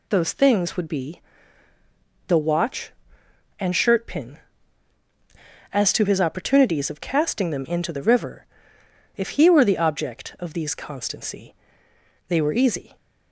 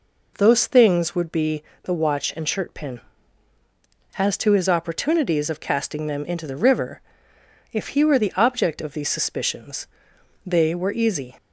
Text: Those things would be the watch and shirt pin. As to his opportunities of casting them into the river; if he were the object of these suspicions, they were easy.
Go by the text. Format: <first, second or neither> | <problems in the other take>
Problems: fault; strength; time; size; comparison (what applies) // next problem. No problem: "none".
second | pauses between "be" and "the"; at 1.1 s; 1.0 s long; slight in the second // says "constancy" for "suspicions"; at 10.7 s